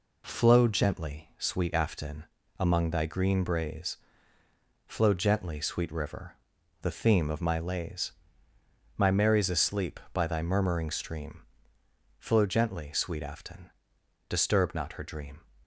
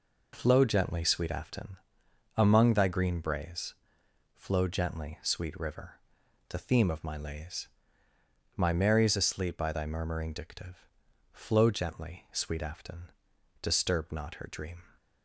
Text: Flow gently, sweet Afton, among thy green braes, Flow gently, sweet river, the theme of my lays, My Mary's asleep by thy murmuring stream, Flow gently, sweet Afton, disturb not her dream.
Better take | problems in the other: first | says "dictive" for "stream"; at 10.3 s

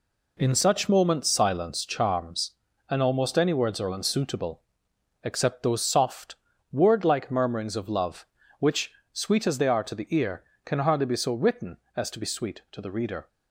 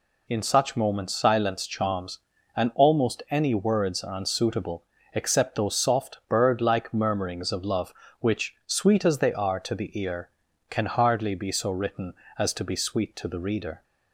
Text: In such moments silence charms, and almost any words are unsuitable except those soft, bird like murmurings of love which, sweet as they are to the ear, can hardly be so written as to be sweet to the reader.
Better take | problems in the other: second | pauses between "unsuitable" and "except"; noticeable; at 4.6 s; 0.62 s long; slight in the second // says "word" for "bird"; at 6.6 s

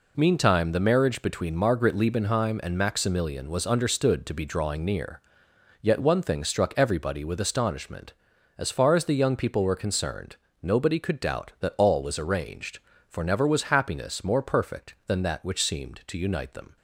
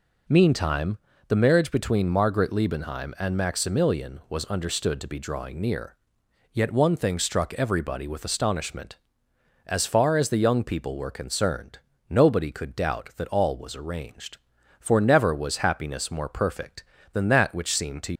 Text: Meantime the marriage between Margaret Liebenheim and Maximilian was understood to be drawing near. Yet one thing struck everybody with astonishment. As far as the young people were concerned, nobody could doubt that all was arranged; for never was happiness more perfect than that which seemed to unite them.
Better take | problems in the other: first | pauses between "Meantime" and "the"; slight; at 0.9 s; 0.30 s long // stops before "unite them"; at 18.1 s

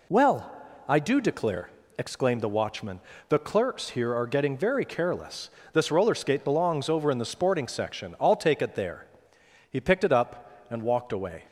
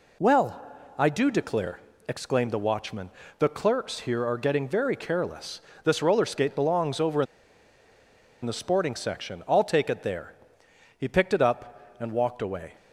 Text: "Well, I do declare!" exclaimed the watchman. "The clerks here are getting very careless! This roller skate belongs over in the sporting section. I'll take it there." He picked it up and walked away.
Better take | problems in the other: first | pauses between "in" and "the"; at 7.2 s; 1.1 s long

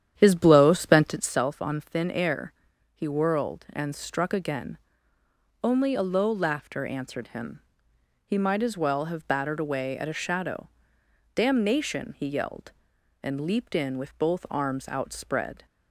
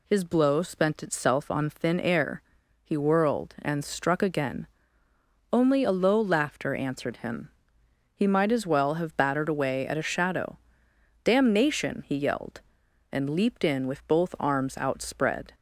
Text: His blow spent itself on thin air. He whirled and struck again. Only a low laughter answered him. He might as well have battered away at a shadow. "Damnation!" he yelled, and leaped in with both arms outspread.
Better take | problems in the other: second | starts louder than the rest; strong; until 1.4 s; 10 dB

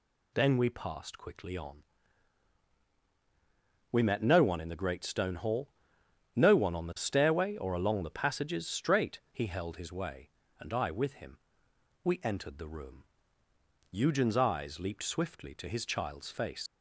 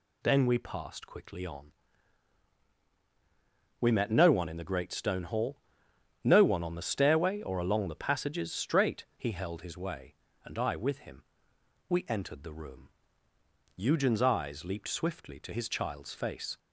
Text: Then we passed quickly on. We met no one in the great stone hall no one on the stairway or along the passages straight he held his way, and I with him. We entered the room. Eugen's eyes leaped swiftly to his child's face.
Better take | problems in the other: second | pauses between "hall" and "no"; noticeable; at 5.6 s; 0.66 s long; noticeable in the second // leaves "face" unfinished; at 16.6 s; 85 ms

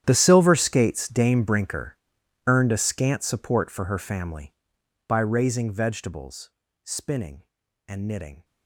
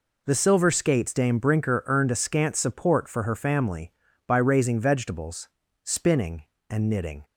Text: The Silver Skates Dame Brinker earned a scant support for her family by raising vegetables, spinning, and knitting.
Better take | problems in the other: second | gets quieter; strong; throughout; 19.5 dB // pauses between "Brinker" and "earned"; noticeable; at 1.9 s; 0.50 s long

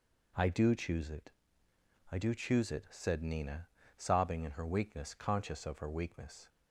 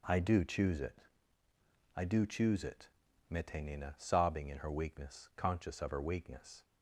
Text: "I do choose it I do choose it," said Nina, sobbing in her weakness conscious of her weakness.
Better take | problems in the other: first | pauses between "it" and "I"; noticeable; at 1.0 s; 0.96 s long; noticeable in the first // says "mete" for "said"; at 3.3 s

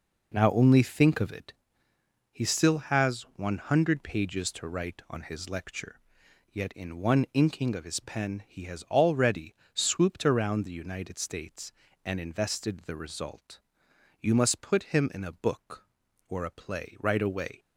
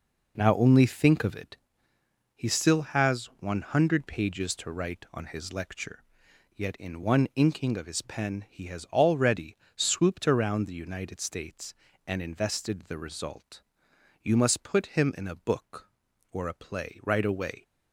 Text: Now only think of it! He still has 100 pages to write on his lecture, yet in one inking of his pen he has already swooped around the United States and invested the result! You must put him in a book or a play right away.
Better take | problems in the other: neither | pauses between "already" and "swooped"; slight; the same in both

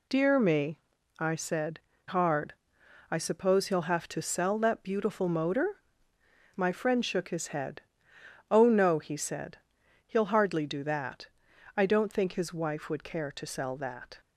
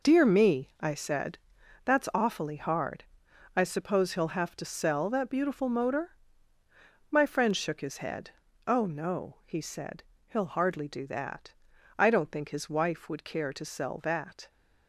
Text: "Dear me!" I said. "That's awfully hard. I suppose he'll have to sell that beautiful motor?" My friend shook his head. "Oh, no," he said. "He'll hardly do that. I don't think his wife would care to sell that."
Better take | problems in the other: second | skips "That's awfully"; at 1.9 s

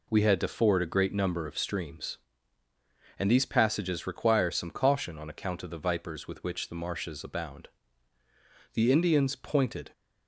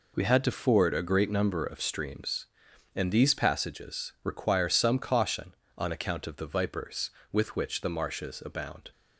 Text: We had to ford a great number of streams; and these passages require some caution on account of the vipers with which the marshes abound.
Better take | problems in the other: second | goes on to say "The Indians pointed"; noticeable; from 8.7 s on; 1.1 s long

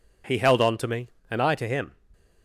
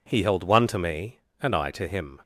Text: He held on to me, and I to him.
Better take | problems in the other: first | says "one" for "on"; at 0.4 s

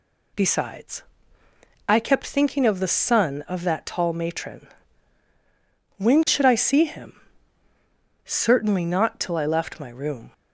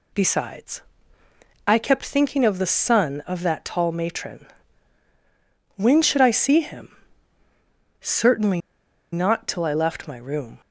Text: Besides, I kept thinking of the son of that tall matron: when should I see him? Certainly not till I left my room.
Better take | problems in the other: first | pauses between "Certainly" and "not"; noticeable; at 8.6 s; 0.52 s long

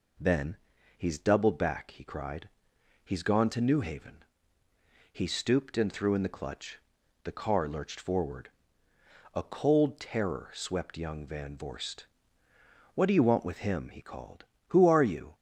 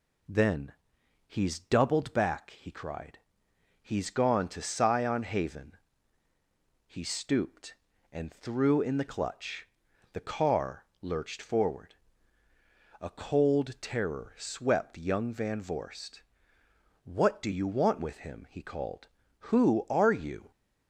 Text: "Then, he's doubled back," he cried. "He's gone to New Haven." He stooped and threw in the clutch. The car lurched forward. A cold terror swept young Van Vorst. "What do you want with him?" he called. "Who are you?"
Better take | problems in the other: first | says "Sion" for "New"; at 4.6 s // pauses between "car" and "lurched"; slight; at 10.8 s; 0.16 s long

